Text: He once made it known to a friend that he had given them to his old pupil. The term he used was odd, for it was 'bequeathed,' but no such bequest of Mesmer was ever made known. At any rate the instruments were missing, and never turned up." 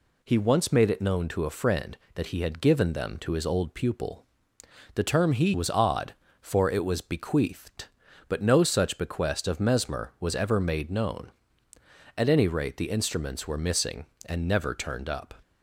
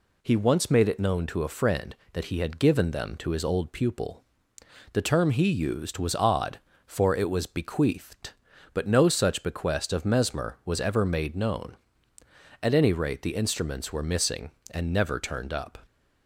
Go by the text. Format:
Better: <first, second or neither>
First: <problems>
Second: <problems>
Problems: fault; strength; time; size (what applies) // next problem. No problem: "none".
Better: second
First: skips "used"; at 5.5 s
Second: none